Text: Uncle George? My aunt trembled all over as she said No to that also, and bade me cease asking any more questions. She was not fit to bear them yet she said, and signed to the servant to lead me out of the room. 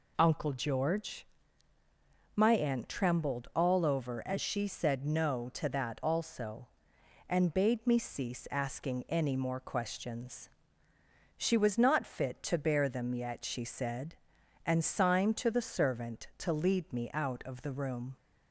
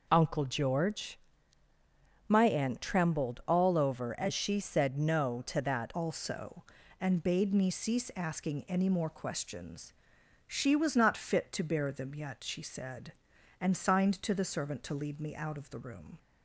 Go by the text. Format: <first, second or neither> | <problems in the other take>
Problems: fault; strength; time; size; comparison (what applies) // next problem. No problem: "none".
first | changes voice at "also"; from 5.9 s on; 10.2 s long